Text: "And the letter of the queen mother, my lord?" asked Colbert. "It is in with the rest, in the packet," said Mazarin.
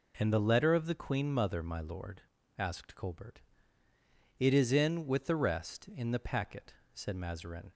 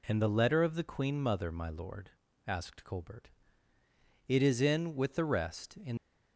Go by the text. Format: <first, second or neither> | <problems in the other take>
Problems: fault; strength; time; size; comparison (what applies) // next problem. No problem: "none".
first | stops before "the packet said Mazarin"; at 5.9 s